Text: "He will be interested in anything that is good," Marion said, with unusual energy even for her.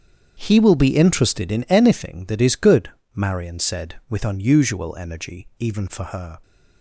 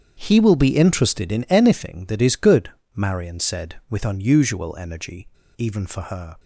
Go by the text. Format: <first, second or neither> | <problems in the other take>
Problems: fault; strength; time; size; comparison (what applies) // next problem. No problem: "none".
first | starts louder than the rest; strong; until 1.2 s; 8 dB; strong in the first // pauses between "energy" and "even"; slight; at 5.2 s; 0.28 s long